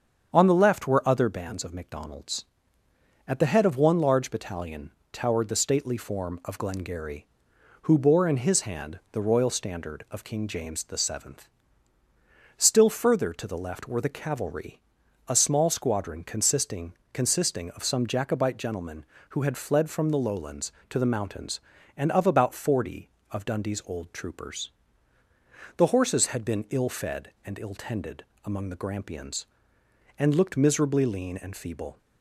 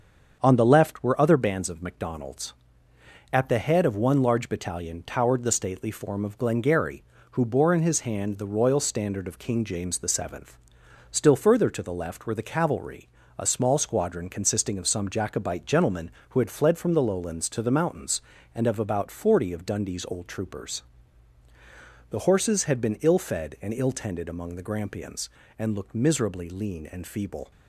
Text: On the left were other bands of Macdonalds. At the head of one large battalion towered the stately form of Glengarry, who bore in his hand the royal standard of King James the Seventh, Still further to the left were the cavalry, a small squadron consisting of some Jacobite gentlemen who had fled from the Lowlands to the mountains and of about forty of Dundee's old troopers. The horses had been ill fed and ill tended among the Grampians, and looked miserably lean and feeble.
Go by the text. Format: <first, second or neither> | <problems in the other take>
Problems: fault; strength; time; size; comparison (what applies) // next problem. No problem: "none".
second | starts louder than the rest; strong; until 1.3 s; 7.5 dB; also in the second // pauses between "battalion" and "towered"; slight; at 4.9 s; 0.22 s long // says "consisting" twice; at 17.1 s // pauses between "tended" and "among"; slight; at 28.2 s; 0.20 s long